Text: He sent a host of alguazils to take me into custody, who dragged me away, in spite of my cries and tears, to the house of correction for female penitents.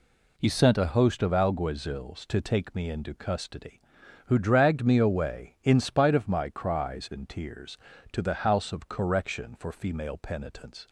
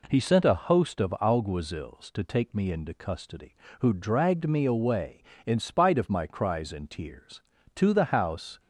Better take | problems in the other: first | stops before "of correction for female penitents"; at 8.5 s

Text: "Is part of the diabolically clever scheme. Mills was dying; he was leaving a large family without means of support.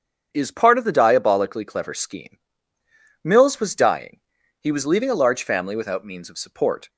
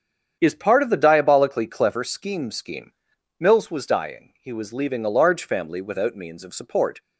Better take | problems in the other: first | starts louder than the rest; strong; until 1.4 s; 8 dB; strong in the first // says "scheme" twice; at 2.5 s

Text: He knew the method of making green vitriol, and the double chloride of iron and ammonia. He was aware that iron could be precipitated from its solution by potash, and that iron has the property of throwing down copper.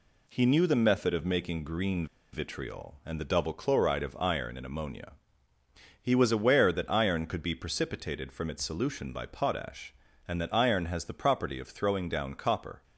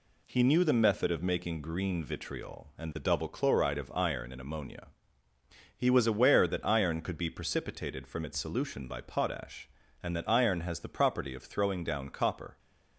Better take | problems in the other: second | pauses between "green" and "vitriol"; slight; at 2.0 s; 0.26 s long

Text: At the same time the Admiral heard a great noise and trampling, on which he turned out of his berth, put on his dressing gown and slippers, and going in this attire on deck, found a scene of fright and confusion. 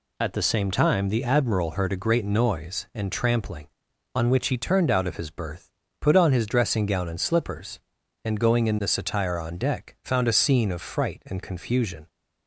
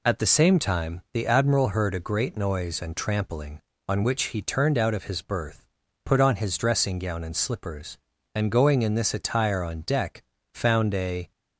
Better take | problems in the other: first | stops before "scene of fright and confusion"; at 11.3 s

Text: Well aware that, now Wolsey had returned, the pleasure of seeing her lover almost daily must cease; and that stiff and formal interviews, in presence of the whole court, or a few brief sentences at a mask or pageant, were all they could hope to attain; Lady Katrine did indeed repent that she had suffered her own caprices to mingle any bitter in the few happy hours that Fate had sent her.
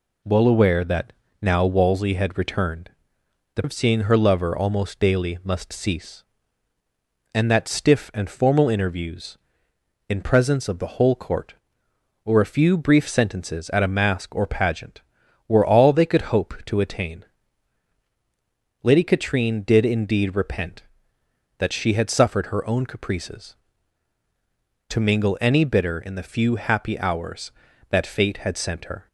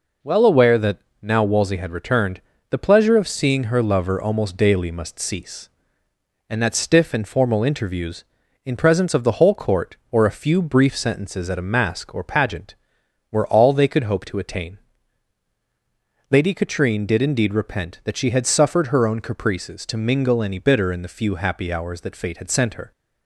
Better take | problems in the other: second | skips "pleasure"; at 3.6 s

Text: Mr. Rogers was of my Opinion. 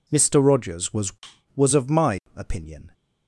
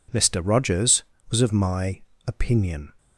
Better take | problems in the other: second | says "was" twice; at 1.5 s // pauses between "my" and "Opinion"; slight; at 2.1 s; 0.18 s long; slight in the second

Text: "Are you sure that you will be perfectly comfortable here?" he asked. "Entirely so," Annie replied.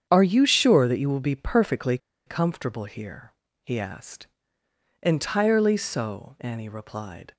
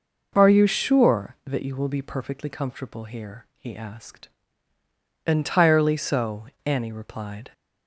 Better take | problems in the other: second | starts louder than the rest; strong; until 1.1 s; 8 dB // pauses between "perfectly" and "comfortable"; slight; at 1.9 s; 0.29 s long

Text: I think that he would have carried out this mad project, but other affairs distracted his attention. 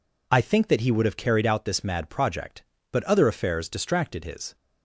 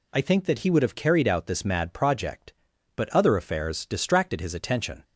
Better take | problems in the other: second | stops before "attention"; at 4.5 s

